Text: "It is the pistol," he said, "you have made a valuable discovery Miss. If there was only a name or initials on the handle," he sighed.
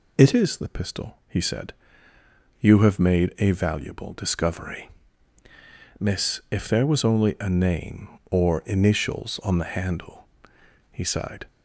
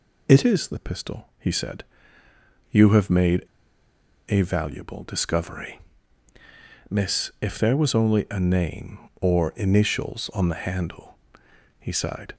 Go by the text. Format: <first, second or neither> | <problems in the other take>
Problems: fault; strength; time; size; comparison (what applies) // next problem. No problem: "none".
first | pauses between "made" and "a"; noticeable; at 3.4 s; 0.82 s long // pauses between "discovery" and "Miss"; at 5.7 s; 1.1 s long; also in the first